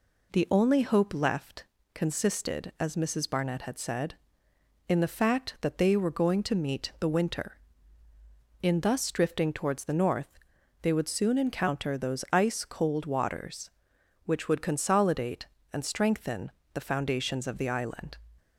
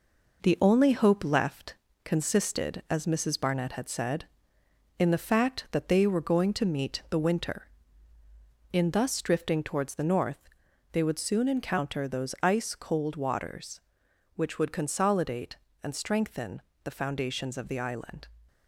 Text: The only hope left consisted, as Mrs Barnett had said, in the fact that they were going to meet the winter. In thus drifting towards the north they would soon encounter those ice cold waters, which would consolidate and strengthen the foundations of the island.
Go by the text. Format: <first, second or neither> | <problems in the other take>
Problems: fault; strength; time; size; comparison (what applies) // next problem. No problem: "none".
first | gets quieter; noticeable; throughout; 5.5 dB // pauses between "left" and "consisted"; slight; at 1.7 s; 0.30 s long; slight in the first // pauses between "north" and "they"; at 10.4 s; 0.44 s long; also in the first // pauses between "strengthen" and "the"; slight; at 16.6 s; 0.22 s long; slight in the first